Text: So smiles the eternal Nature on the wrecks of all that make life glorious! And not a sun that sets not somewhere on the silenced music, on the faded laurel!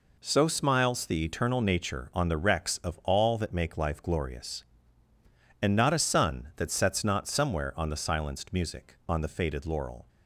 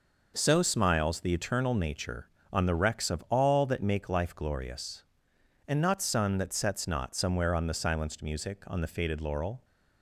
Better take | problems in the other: first | skips "a"; at 6.0 s

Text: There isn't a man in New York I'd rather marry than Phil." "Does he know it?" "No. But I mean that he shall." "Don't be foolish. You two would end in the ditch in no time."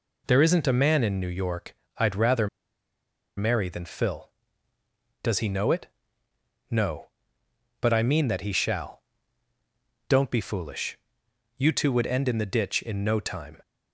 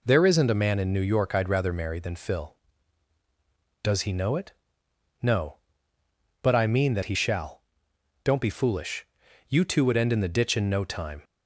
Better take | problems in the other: second | pauses between "York" and "I'd"; slight; at 1.7 s; 0.22 s long // pauses between "rather" and "marry"; noticeable; at 2.4 s; 0.89 s long

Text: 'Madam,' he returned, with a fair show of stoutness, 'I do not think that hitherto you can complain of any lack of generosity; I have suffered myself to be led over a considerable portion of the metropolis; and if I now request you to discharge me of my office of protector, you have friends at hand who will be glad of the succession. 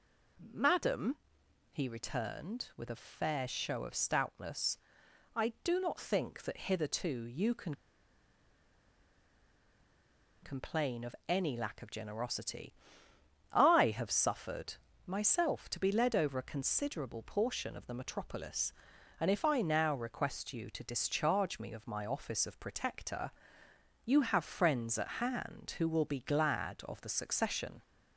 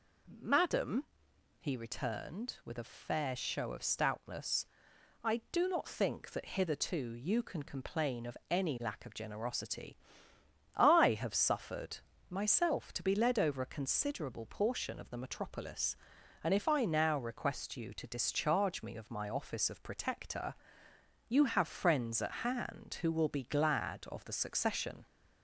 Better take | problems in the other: second | pauses between "can" and "complain"; strong; at 7.7 s; 2.6 s long // pauses between "suffered" and "myself"; slight; at 14.7 s; 0.30 s long; slight in the second

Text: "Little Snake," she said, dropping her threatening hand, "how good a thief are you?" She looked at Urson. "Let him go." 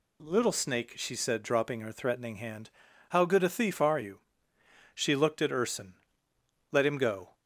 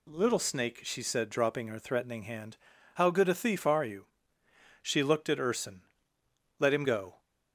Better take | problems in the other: neither | none

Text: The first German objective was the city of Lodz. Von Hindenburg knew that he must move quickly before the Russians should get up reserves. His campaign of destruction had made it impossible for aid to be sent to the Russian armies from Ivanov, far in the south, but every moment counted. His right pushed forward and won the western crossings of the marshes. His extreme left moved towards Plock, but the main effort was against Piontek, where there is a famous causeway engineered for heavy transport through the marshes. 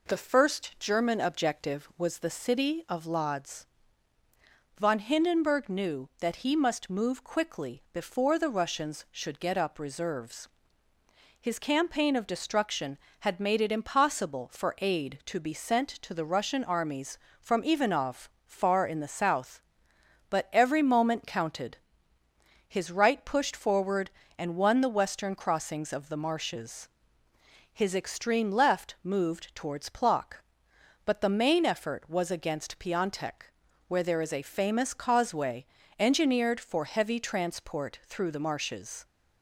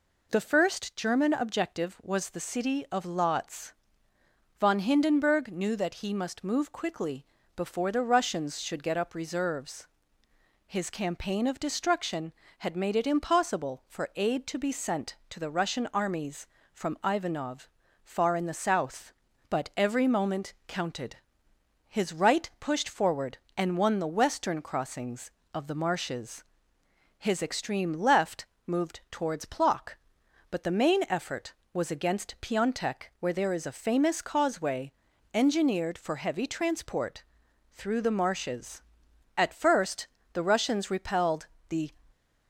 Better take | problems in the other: first | pauses between "quickly" and "before"; slight; at 7.2 s; 0.32 s long // pauses between "moment" and "counted"; slight; at 20.5 s; 0.16 s long // pauses between "left" and "moved"; slight; at 28.4 s; 0.20 s long // pauses between "causeway" and "engineered"; at 34.9 s; 0.42 s long; slight in the first // pauses between "transport" and "through"; noticeable; at 37.2 s; 0.50 s long // goes on to say "At first the Russians repelled the"; strong; from 39.3 s on; 2.5 s long

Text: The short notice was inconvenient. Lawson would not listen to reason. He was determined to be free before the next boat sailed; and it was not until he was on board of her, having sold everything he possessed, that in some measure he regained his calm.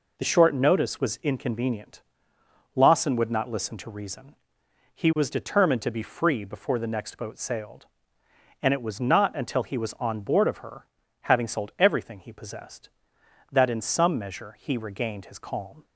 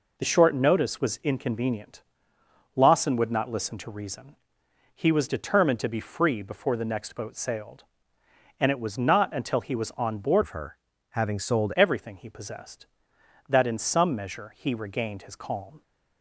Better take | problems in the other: first | changes voice from "of" to "sold"; from 10.4 to 11.7 s; 1.3 s long

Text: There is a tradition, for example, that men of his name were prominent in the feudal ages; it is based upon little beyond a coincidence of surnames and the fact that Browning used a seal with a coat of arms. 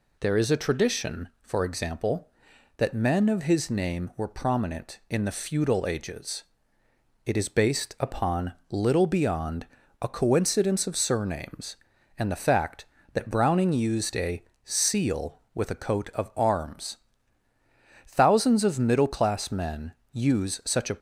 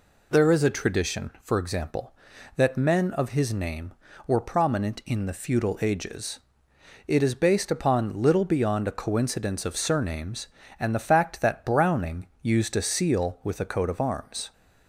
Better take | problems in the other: second | pauses between "upon" and "little"; slight; at 8.5 s; 0.18 s long // pauses between "beyond" and "a"; slight; at 9.6 s; 0.34 s long // pauses between "a" and "seal"; slight; at 14.4 s; 0.22 s long // goes on to say "Thousands of middle class men use such a"; strong; from 18.0 s on; 2.8 s long

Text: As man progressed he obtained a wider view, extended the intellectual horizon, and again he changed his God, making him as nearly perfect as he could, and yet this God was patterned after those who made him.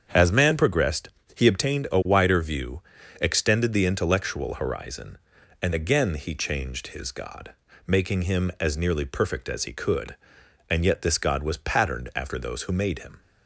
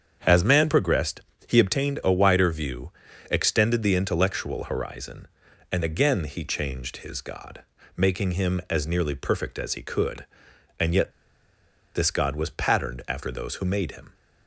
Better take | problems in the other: first | starts louder than the rest; strong; until 1.5 s; 7.5 dB; strong in the first // pauses between "progressed" and "he"; slight; at 1.2 s; 0.26 s long; slight in the first // pauses between "yet" and "this"; noticeable; at 11.1 s; 0.84 s long

